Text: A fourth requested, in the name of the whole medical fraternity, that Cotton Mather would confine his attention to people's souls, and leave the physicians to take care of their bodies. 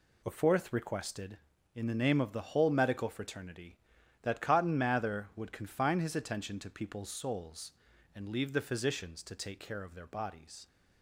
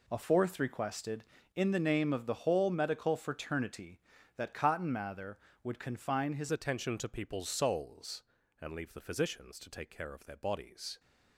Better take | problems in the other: first | changes voice at "attention"; from 6.5 s on; 4.4 s long

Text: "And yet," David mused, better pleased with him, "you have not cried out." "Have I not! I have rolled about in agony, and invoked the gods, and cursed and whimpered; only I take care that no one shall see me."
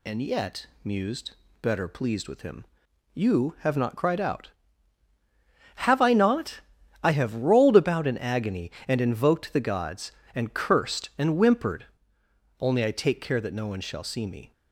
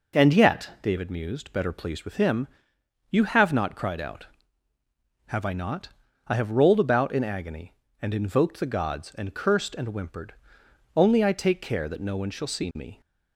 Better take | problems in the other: second | skips "David"; at 0.7 s

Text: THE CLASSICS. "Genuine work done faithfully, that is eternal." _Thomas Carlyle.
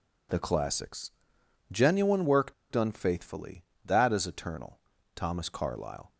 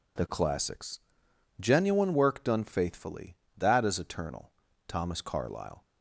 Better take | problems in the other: second | pauses between "work" and "done"; slight; at 2.5 s; 0.16 s long

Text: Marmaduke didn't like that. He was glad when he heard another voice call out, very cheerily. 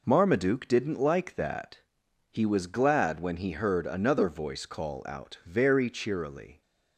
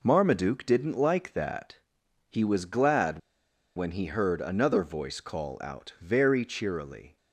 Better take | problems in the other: first | pauses between "glad" and "when"; noticeable; at 3.1 s; 0.57 s long

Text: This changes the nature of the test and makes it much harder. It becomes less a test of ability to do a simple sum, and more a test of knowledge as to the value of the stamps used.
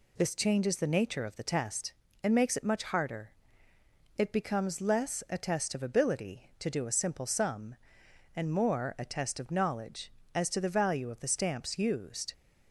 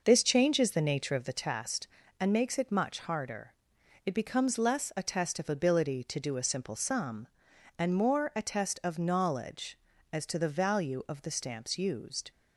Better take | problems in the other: first | starts louder than the rest; noticeable; until 1.3 s; 5.5 dB

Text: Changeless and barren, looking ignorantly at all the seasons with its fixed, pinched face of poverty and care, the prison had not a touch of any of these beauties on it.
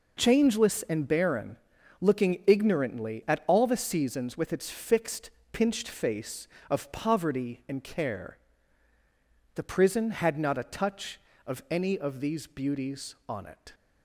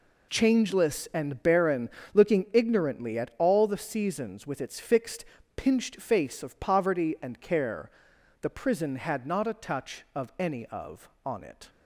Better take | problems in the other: first | skips "these beauties"; at 11.1 s

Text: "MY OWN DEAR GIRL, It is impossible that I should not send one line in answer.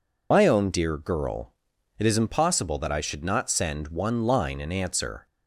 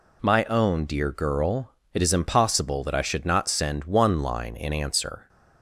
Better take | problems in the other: second | loses the start of "MY"; at 0.3 s; 70 ms

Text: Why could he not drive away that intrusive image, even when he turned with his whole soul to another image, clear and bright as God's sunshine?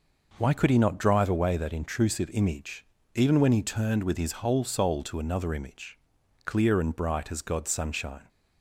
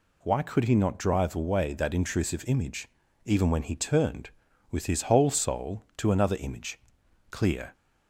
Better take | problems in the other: first | stops before "and bright as God's sunshine"; at 7.7 s

